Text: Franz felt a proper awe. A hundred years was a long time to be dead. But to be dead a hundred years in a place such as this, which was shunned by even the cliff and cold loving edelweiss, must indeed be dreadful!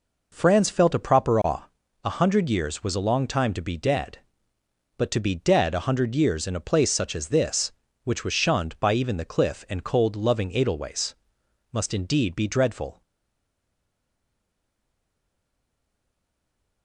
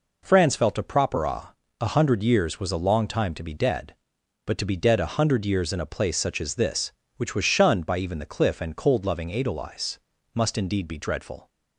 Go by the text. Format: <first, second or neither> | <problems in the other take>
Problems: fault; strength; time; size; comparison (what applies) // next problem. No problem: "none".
second | stays silent after the last word; strong; from 13.0 s on; 3.8 s long